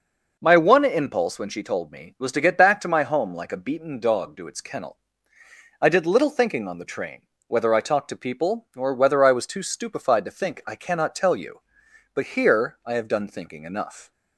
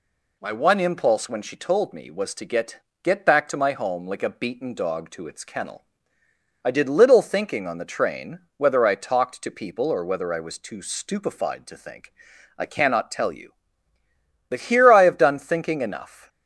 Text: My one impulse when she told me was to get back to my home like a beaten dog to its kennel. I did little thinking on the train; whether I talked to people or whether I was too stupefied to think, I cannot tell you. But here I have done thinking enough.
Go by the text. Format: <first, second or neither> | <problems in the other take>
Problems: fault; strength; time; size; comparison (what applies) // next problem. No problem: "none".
first | says "get" twice; at 3.0 s